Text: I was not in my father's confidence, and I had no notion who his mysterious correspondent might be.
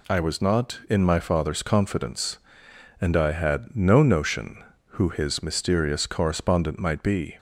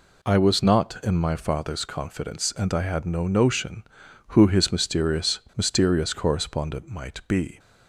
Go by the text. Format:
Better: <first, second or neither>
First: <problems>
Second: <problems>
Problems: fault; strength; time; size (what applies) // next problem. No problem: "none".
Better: first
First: none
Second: says "mysterious" twice; at 5.5 s